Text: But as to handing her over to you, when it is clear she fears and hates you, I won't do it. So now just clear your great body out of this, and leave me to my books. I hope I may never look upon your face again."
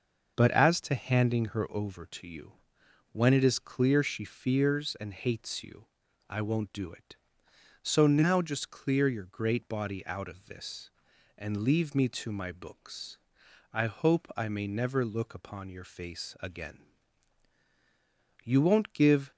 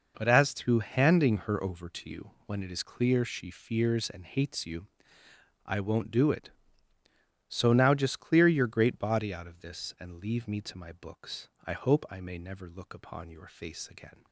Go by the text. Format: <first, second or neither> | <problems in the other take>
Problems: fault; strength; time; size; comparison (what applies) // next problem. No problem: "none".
second | starts louder than the rest; until 1.3 s; 6 dB // goes on to say "You won't give"; noticeable; from 18.4 s on; 0.88 s long